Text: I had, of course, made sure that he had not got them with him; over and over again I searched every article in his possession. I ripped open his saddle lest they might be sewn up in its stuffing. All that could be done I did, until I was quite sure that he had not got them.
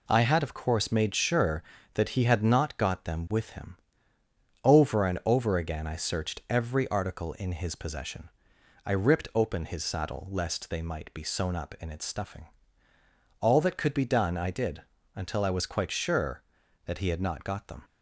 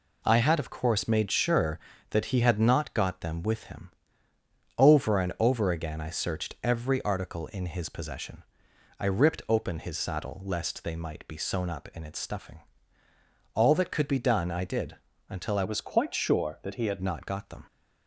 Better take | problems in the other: first | changes voice from "was" to "had"; from 15.6 to 17.0 s; 1.4 s long

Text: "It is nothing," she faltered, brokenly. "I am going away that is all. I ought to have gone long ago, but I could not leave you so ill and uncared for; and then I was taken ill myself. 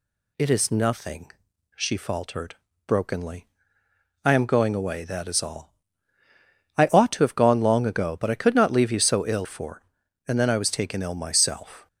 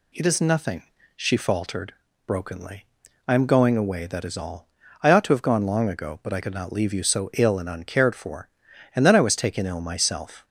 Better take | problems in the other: second | skips "and uncared"; at 9.4 s

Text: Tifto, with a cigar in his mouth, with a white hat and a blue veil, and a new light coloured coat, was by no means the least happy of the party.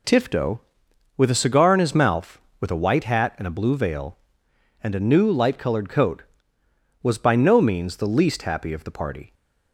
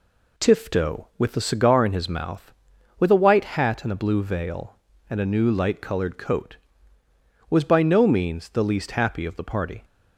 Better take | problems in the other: neither | none

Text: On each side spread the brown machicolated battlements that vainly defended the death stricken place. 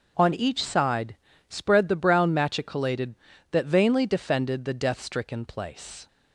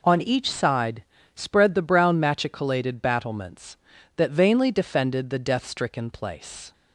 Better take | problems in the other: second | pauses between "side" and "spread"; slight; at 1.1 s; 0.32 s long; slight in the second // skips "battlements"; at 3.3 s

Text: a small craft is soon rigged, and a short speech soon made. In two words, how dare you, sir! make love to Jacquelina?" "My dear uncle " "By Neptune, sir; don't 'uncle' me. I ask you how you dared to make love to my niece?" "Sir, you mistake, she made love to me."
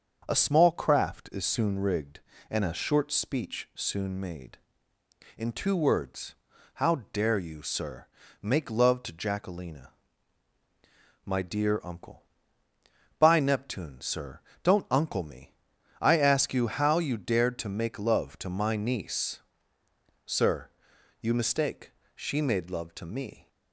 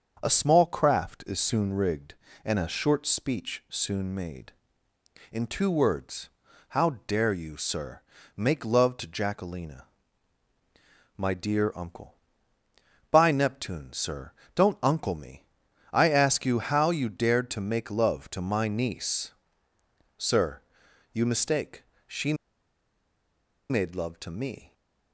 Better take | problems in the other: first | starts louder than the rest; until 1.2 s; 6.5 dB; also in the first // pauses between "she" and "made"; strong; at 22.3 s; 1.3 s long

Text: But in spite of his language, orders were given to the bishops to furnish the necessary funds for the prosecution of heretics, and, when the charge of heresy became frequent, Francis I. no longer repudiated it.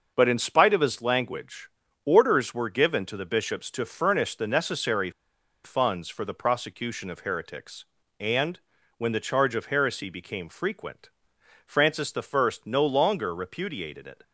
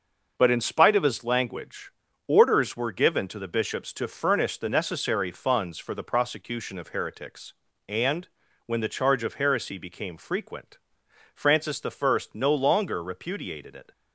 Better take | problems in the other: second | starts louder than the rest; noticeable; until 1.1 s; 6 dB // pauses between "necessary" and "funds"; noticeable; at 5.0 s; 0.54 s long

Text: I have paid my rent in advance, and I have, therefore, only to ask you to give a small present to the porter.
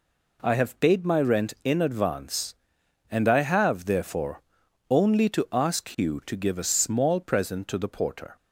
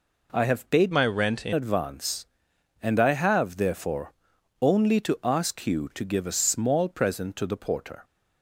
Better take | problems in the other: first | changes voice from "my" to "in"; from 0.9 to 1.5 s; 0.6 s long

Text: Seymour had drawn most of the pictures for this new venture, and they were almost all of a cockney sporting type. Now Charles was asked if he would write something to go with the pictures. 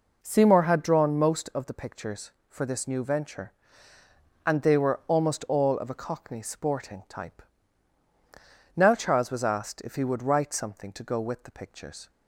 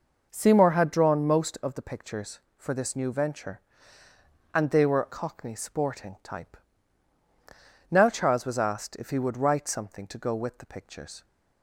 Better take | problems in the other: first | skips "almost all of a"; at 5.0 s

